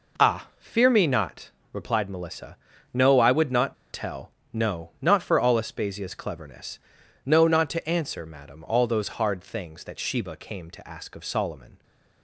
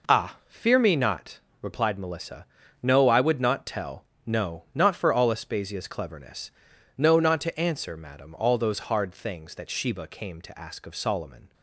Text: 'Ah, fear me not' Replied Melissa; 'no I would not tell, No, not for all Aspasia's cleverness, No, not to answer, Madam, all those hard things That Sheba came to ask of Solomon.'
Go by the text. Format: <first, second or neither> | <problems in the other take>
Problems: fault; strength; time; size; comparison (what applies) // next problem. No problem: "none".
second | pauses between "not" and "Replied"; slight; at 1.5 s; 0.22 s long; slight in the second // pauses between "not" and "tell"; slight; at 3.7 s; 0.17 s long